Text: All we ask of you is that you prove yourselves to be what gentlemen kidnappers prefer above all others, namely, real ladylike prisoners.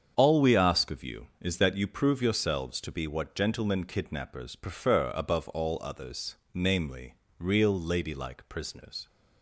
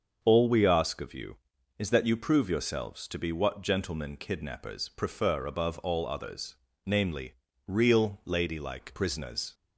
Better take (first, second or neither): neither